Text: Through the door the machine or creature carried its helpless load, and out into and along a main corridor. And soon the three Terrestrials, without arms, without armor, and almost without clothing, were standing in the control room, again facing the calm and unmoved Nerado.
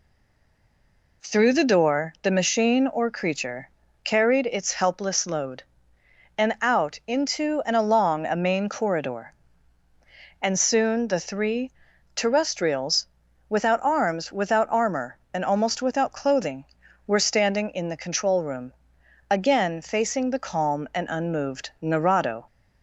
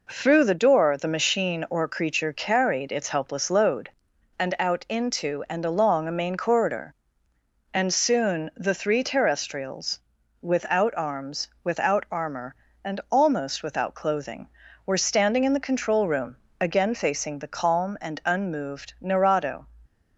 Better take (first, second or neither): second